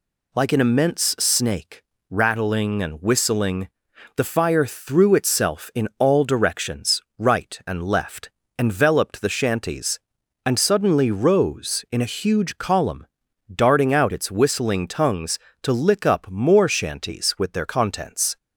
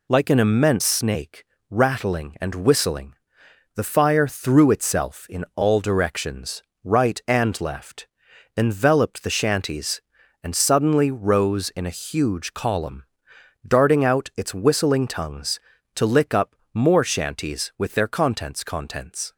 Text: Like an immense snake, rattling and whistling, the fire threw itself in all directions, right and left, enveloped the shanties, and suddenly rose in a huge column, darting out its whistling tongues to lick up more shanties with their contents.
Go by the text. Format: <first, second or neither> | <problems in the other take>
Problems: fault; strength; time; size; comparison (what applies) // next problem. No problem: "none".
first | pauses between "up" and "more"; slight; at 16.5 s; 0.18 s long // says "contents" twice; at 18.6 s